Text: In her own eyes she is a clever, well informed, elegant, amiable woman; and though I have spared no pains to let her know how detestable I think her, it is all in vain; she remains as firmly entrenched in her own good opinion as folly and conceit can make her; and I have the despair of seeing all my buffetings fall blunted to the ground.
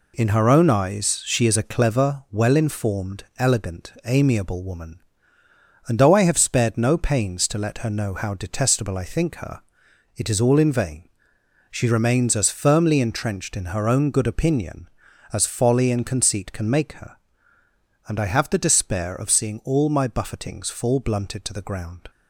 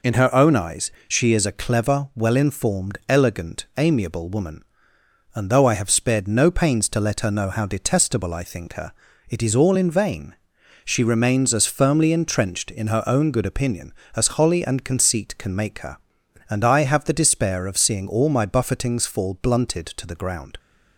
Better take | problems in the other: first | pauses between "eyes" and "she"; slight; at 0.9 s; 0.16 s long // says "holly" for "folly"; at 14.3 s

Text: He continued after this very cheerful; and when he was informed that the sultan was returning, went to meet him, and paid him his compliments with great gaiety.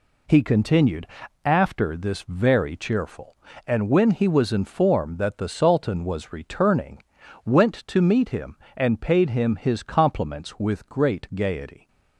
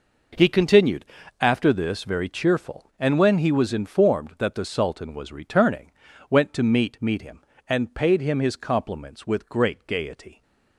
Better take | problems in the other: first | pauses between "continued" and "after"; slight; at 1.0 s; 0.34 s long; also in the first // says "meet" twice; at 6.9 s

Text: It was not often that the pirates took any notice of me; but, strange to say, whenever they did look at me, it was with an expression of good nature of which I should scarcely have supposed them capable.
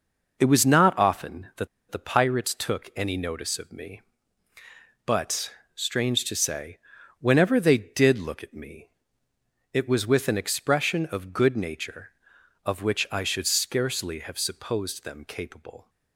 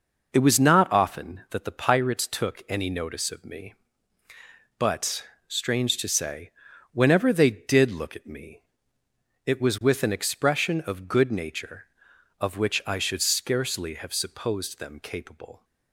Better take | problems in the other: second | pauses between "that" and "the"; slight; at 1.6 s; 0.23 s long

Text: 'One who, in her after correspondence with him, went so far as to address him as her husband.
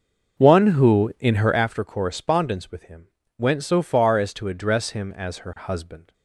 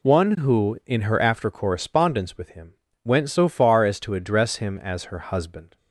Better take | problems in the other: second | starts louder than the rest; until 1.6 s; 6 dB

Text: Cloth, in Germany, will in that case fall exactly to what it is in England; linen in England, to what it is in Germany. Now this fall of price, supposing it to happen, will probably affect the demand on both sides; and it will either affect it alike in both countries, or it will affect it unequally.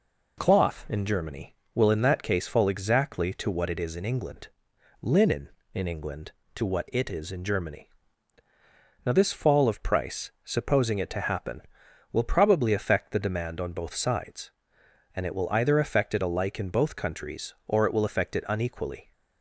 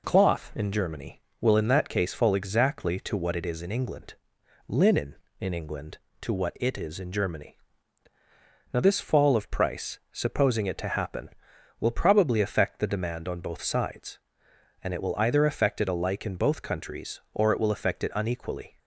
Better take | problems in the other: neither | none

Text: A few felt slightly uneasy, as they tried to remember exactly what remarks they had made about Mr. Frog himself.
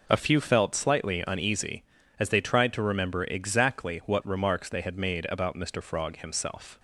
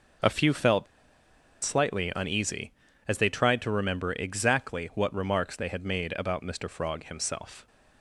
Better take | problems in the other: first | pauses between "felt" and "slightly"; noticeable; at 0.8 s; 0.78 s long

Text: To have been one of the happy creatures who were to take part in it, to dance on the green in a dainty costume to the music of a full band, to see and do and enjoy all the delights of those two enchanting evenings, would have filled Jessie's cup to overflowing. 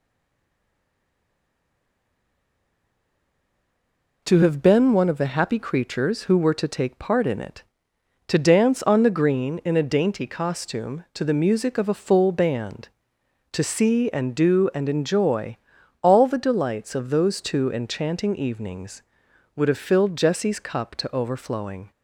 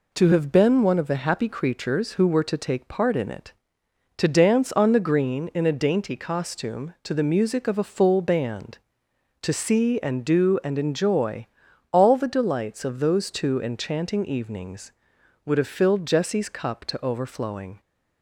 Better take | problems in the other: second | stays silent before the first word; strong; until 4.2 s; 4.2 s long // pauses between "enjoy" and "all"; noticeable; at 15.5 s; 0.46 s long; noticeable in the second

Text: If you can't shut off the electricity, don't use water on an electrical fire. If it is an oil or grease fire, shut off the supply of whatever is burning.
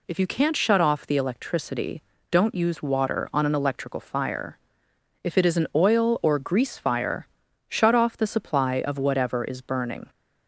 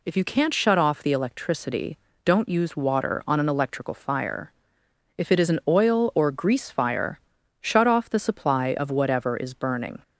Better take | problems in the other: neither | none

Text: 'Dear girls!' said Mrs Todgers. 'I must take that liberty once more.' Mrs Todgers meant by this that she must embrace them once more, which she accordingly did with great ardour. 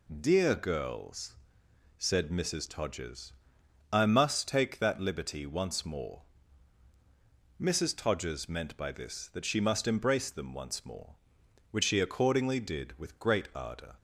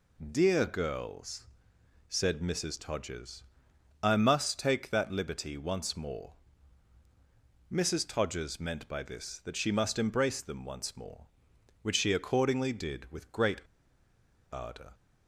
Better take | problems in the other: first | pauses between "great" and "ardour"; noticeable; at 13.5 s; 0.92 s long

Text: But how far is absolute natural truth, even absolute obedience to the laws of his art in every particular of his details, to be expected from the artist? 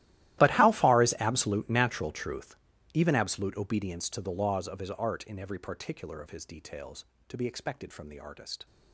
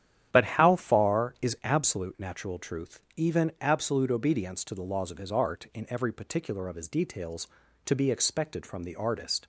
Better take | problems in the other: second | gets quieter; strong; throughout; 20.5 dB // starts louder than the rest; strong; until 1.4 s; 15 dB; strong in the second

